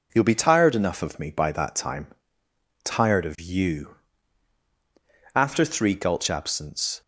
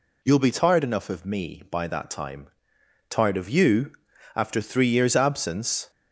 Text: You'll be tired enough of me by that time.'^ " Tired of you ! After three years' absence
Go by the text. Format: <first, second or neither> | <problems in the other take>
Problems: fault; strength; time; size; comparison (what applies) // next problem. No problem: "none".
second | says "gulch" for "years"; at 5.9 s